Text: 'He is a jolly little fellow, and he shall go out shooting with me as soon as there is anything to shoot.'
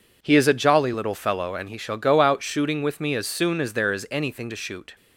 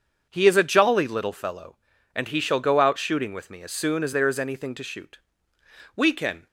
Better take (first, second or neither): first